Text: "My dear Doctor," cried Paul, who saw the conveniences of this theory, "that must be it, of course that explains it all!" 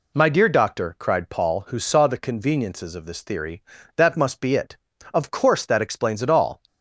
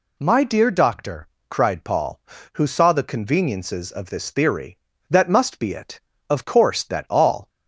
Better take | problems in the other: first | skips "explains it"; at 7.0 s

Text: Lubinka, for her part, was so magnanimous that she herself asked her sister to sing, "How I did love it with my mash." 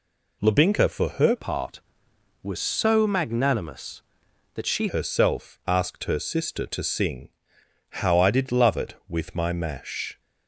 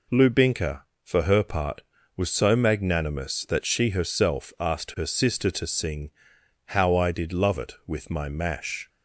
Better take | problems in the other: second | changes voice from "part" to "she"; from 1.3 to 4.8 s; 3.5 s long

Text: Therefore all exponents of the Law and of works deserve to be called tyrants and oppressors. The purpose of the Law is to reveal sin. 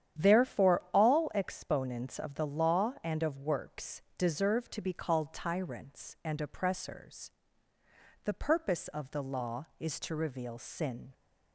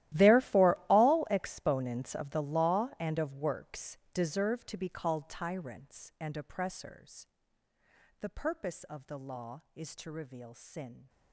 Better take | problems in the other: first | gets quieter; strong; throughout; 19.5 dB // starts louder than the rest; strong; until 1.3 s; 14.5 dB; strong in the first // pauses between "works" and "deserve"; slight; at 3.9 s; 0.16 s long; slight in the first

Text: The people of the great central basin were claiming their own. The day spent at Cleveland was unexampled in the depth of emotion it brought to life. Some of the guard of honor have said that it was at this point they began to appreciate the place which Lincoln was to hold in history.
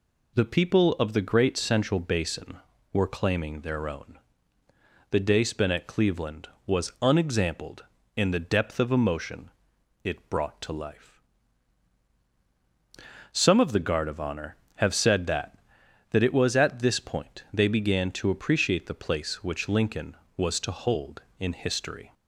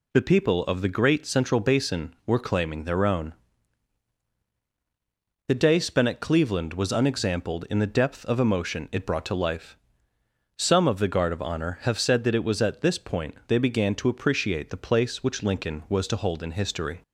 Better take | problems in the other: second | pauses between "emotion" and "it"; noticeable; at 9.5 s; 0.52 s long // says "that" twice; at 16.0 s

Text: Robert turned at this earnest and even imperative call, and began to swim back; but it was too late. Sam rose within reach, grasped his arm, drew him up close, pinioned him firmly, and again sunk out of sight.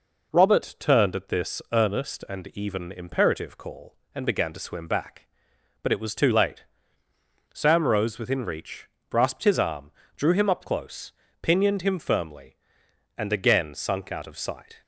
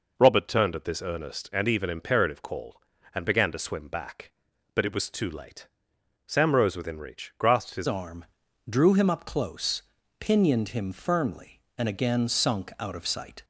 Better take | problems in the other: first | changes voice at "arm"; from 7.8 s on; 5.6 s long

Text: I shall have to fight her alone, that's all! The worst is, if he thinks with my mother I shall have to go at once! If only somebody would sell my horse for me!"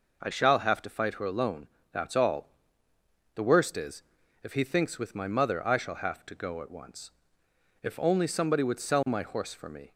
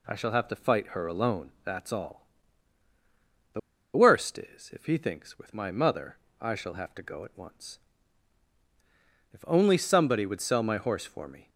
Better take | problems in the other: first | pauses between "The" and "worst"; at 3.5 s; 0.36 s long // pauses between "mother" and "I"; slight; at 6.1 s; 0.24 s long

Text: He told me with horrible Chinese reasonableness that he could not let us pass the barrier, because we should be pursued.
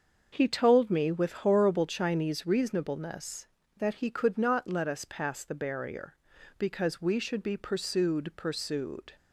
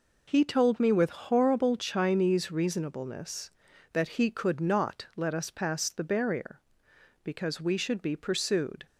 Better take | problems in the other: second | starts louder than the rest; until 1.3 s; 6.5 dB // says "pursued" twice; at 8.3 s

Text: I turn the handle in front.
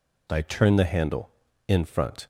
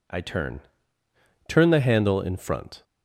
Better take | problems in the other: first | says "turn" twice; at 1.4 s

